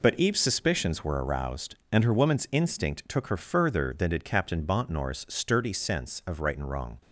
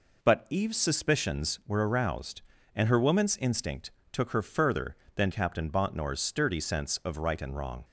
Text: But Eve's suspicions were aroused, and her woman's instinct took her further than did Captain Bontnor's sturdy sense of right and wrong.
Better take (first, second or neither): first